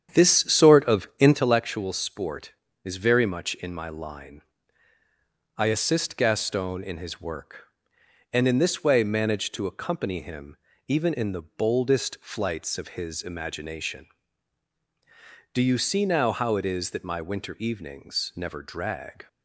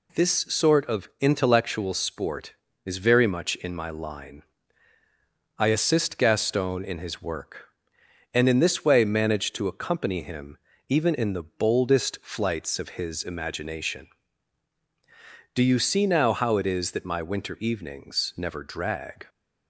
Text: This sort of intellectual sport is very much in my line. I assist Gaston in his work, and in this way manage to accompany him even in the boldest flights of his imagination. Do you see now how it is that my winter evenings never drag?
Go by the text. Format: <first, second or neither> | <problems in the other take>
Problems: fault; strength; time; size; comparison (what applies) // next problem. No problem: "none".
second | starts louder than the rest; strong; until 1.4 s; 9 dB // pauses between "him" and "even"; slight; at 10.5 s; 0.32 s long; slight in the second